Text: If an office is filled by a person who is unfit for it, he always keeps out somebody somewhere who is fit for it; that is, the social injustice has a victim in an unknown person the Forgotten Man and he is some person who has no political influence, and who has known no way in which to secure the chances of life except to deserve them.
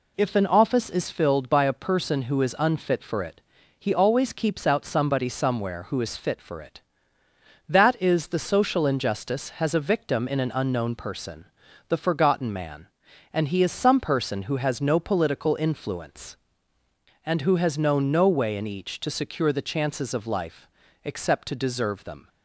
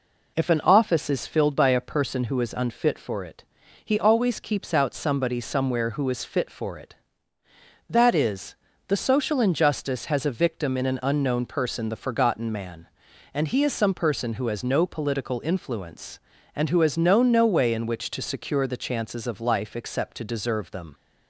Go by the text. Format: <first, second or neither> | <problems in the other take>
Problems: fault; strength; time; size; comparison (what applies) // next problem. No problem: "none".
second | pauses between "person" and "the"; at 11.4 s; 0.42 s long // says "each" for "which"; at 18.6 s // pauses between "life" and "except"; slight; at 20.6 s; 0.36 s long